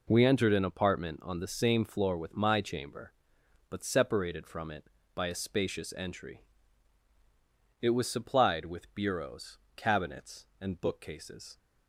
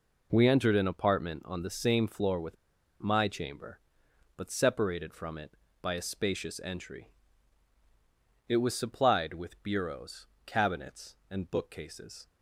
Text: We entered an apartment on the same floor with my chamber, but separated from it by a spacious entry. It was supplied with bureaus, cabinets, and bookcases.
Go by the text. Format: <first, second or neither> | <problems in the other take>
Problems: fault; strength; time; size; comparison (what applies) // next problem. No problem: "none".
first | pauses between "with" and "my"; at 2.5 s; 0.45 s long